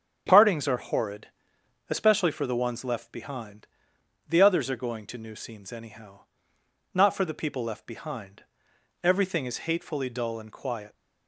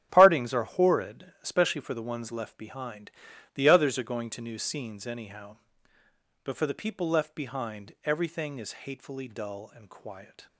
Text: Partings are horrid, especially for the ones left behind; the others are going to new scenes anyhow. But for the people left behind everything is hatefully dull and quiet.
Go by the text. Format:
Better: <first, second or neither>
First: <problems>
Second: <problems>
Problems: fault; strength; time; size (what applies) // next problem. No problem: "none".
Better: second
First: starts louder than the rest; strong; until 1.2 s; 8 dB // says "Not" for "But"; at 6.9 s // pauses between "behind" and "everything"; noticeable; at 8.4 s; 0.60 s long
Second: starts louder than the rest; strong; until 1.1 s; 9.5 dB